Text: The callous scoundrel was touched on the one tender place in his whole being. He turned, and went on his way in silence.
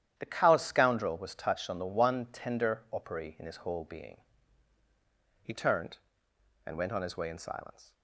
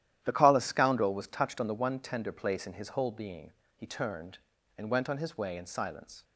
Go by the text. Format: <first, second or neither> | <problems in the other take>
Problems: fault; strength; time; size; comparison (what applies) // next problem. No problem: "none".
second | starts louder than the rest; strong; until 1.1 s; 10.5 dB; strong in the second // says "opery" for "place"; at 2.8 s